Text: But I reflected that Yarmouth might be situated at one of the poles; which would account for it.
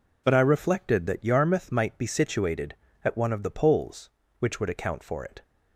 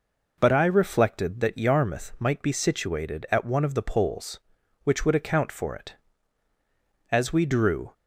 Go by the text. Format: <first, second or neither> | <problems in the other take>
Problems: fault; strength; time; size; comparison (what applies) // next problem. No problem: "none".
first | goes on to say "As we drew"; noticeable; from 7.1 s on; 0.82 s long